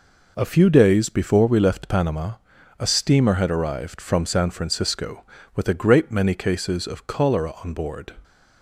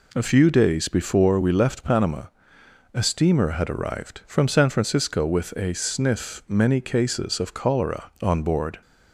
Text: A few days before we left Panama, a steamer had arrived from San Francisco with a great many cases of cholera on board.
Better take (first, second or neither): first